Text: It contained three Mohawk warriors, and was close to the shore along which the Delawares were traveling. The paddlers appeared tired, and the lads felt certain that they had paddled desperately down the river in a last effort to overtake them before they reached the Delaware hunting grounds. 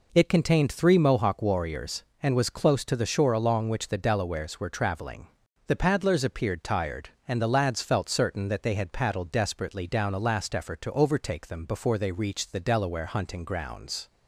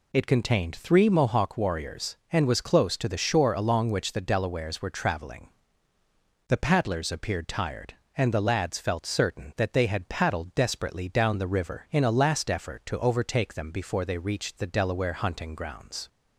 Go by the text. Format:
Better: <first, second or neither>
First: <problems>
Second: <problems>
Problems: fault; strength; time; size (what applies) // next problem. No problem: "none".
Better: second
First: skips "the river in"; at 10.1 s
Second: none